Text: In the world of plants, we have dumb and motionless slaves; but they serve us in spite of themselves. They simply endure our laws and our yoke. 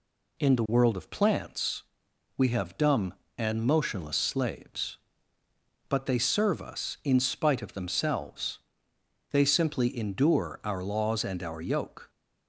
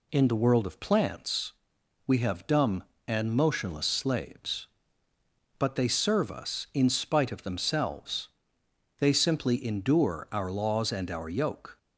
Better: neither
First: none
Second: none

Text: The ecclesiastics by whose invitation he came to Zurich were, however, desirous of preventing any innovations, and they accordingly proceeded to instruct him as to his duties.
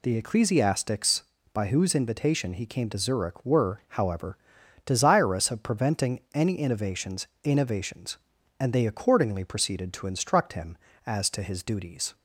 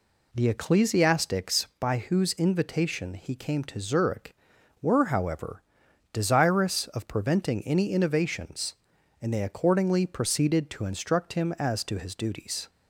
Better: second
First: says "innovations" twice; at 7.4 s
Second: none

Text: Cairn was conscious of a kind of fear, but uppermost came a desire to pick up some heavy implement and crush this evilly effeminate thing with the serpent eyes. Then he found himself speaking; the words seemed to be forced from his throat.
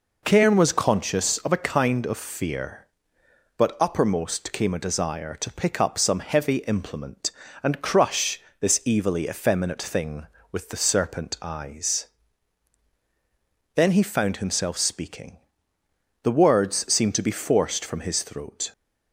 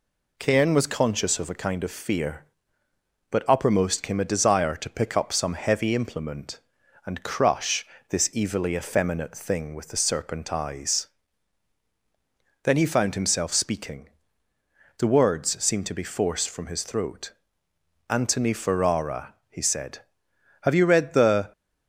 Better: first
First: pauses between "crush" and "this"; slight; at 8.3 s; 0.20 s long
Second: pauses between "crush" and "this"; slight; at 7.8 s; 0.24 s long // goes on to say "Antony Ferrara he said have you read the"; strong; from 18.0 s on; 3.4 s long

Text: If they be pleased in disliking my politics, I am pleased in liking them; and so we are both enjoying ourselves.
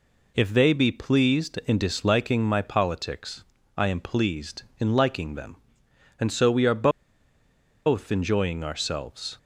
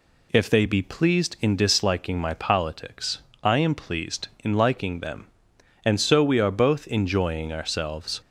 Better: second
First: pauses between "are" and "both"; noticeable; at 6.8 s; 0.97 s long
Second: none

